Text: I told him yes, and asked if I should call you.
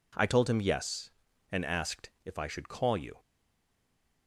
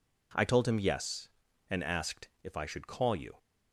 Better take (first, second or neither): second